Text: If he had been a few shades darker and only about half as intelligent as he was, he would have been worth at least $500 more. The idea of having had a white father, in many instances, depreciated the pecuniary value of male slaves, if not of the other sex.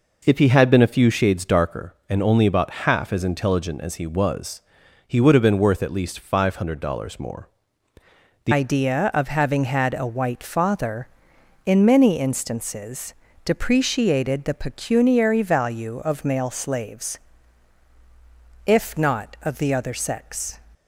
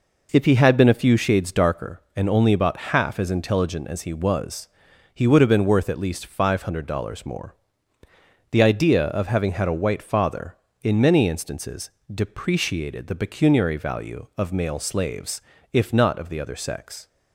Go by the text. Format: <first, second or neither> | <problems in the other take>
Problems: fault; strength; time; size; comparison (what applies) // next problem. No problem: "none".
second | changes voice at "idea"; from 8.5 s on; 12.0 s long